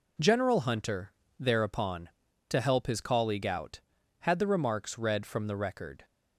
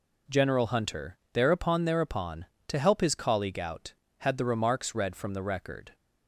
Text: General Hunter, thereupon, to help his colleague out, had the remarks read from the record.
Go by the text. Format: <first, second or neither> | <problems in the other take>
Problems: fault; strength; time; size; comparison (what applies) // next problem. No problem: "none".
first | says "thereupon" twice; at 1.8 s